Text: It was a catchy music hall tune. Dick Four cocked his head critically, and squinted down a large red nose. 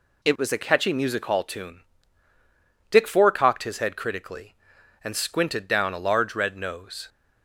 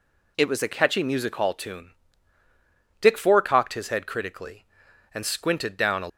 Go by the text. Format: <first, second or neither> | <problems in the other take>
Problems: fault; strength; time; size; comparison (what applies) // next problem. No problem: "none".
first | stops before "large red nose"; at 6.0 s